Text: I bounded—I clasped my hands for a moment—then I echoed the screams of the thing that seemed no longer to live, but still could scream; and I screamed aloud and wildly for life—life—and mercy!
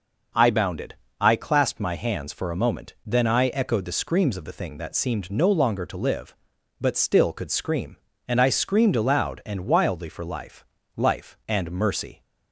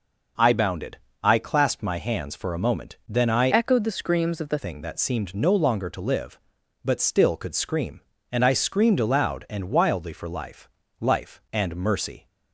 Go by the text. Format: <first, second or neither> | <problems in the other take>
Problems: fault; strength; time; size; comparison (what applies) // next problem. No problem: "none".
first | changes voice from "echoed" to "the"; from 3.5 to 4.5 s; 1.0 s long